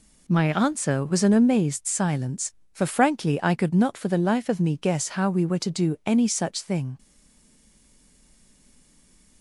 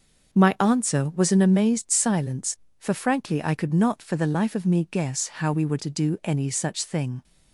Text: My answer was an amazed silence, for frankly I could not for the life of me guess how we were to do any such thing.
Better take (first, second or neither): second